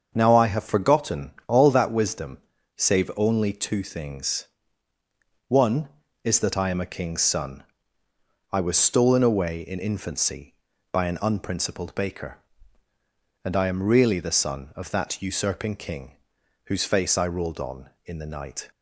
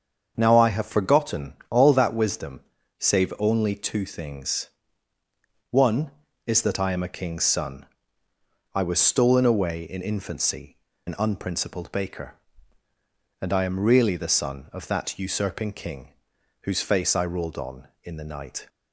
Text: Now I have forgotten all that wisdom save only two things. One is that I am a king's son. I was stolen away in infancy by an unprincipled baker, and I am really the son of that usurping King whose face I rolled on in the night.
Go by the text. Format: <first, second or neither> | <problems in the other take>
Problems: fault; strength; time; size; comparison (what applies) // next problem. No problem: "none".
first | starts louder than the rest; until 1.3 s; 7 dB; also in the first // pauses between "forgotten" and "all"; slight; at 1.5 s; 0.16 s long; slight in the first // pauses between "wisdom" and "save"; at 2.5 s; 0.38 s long; also in the first // skips "by"; at 10.9 s // pauses between "King" and "whose"; noticeable; at 16.0 s; 0.54 s long; noticeable in the first